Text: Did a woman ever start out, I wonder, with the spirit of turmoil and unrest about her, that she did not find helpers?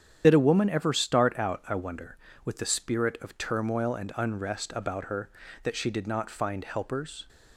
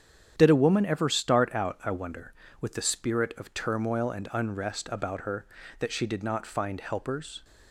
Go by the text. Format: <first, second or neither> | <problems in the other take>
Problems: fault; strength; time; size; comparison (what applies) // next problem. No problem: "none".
second | loses the start of "Did"; at 0.2 s; 30 ms // starts louder than the rest; strong; until 1.2 s; 9 dB; strong in the second